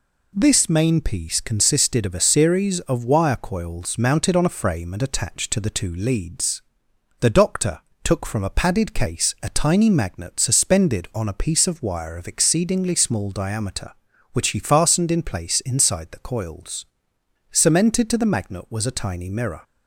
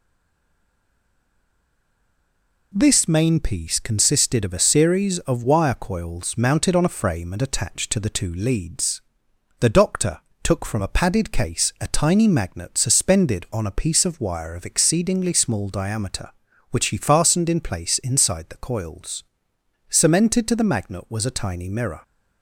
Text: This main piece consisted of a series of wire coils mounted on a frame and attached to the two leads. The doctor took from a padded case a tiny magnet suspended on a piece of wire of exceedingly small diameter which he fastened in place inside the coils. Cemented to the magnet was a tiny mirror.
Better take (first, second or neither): first